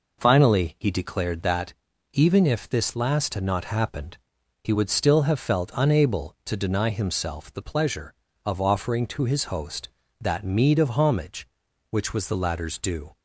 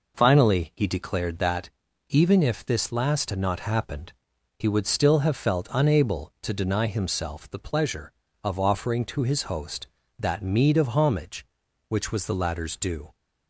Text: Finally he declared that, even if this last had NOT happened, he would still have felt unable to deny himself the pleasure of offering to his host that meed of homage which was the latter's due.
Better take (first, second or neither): neither